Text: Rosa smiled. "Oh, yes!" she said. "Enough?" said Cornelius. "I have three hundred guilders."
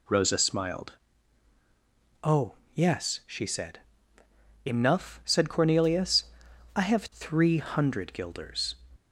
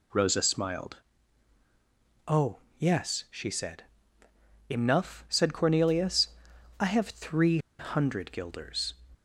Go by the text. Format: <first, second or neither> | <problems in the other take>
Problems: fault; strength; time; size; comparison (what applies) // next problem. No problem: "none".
first | pauses between "three" and "hundred"; slight; at 7.5 s; 0.20 s long